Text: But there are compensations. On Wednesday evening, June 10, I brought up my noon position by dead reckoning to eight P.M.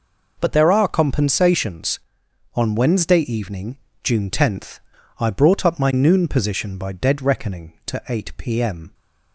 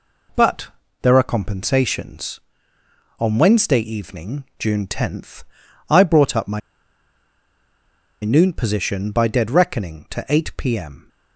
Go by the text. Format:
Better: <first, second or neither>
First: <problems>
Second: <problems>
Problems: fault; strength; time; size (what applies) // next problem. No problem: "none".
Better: first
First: none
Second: pauses between "But" and "there"; slight; at 0.6 s; 0.34 s long // pauses between "my" and "noon"; strong; at 6.6 s; 1.6 s long